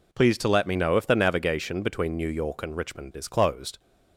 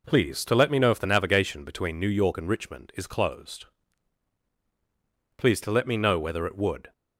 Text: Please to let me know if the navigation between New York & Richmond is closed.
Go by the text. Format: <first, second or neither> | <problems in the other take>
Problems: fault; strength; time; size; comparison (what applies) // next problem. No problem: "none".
first | goes on to say "Please to let me know whether it would"; from 5.3 s on; 1.5 s long